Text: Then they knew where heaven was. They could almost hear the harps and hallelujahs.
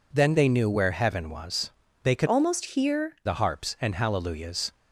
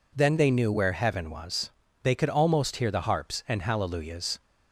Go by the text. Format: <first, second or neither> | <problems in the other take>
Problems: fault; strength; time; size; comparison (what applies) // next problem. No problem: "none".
second | changes voice from "almost" to "hear"; from 2.2 to 3.1 s; 0.9 s long